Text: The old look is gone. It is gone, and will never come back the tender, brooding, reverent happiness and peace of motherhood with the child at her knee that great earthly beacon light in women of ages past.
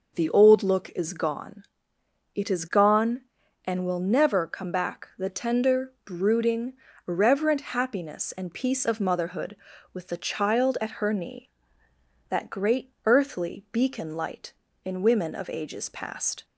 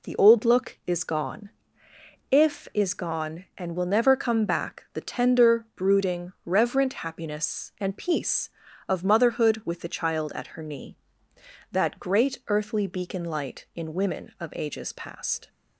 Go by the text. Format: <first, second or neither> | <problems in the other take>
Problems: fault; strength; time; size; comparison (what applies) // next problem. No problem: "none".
first | says "If" for "It"; at 2.2 s